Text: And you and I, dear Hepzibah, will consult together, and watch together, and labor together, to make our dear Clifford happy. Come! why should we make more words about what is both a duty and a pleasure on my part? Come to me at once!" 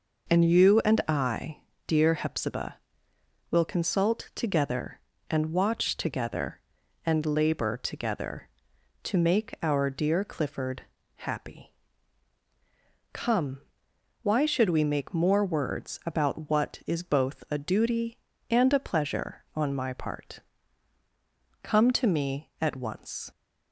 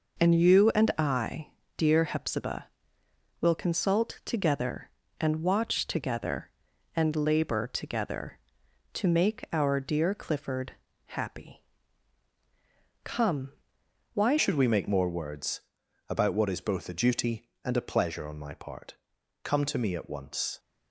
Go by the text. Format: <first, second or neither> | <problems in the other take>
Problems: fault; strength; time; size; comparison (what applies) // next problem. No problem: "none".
first | pauses between "Clifford" and "happy"; slight; at 10.7 s; 0.34 s long; slight in the first // changes voice at "should"; from 14.3 s on; 6.2 s long // pauses between "words" and "about"; noticeable; at 15.6 s; 0.48 s long